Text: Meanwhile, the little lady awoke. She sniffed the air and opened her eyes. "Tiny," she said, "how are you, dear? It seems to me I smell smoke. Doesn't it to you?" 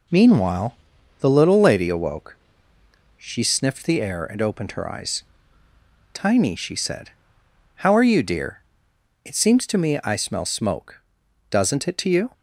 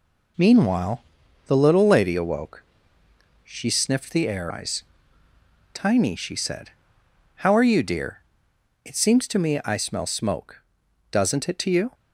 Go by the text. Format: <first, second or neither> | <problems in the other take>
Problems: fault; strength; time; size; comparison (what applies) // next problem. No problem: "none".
first | skips "and opened her"; at 4.5 s